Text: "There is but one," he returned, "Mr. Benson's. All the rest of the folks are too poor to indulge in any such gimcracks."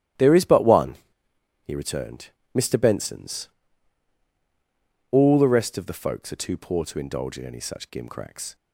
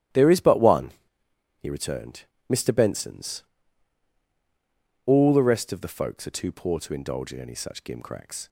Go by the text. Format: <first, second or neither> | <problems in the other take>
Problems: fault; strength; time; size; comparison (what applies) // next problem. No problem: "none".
neither | starts louder than the rest; strong; the same in both